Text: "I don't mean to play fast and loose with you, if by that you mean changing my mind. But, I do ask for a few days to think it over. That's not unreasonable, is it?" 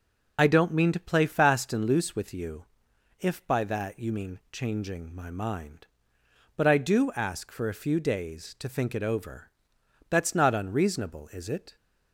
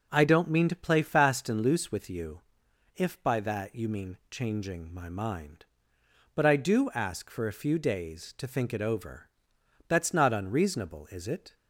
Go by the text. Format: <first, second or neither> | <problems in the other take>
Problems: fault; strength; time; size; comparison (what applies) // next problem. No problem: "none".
second | loses the start of "I"; at 0.3 s; 60 ms